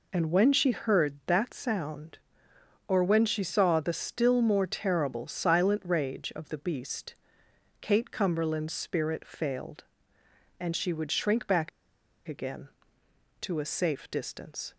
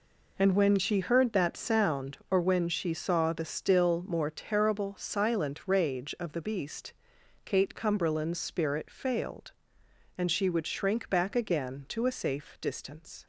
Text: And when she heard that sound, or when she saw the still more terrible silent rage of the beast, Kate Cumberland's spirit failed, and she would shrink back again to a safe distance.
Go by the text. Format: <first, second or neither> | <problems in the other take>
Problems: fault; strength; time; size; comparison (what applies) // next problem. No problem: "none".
second | pauses between "back" and "again"; noticeable; at 11.6 s; 0.58 s long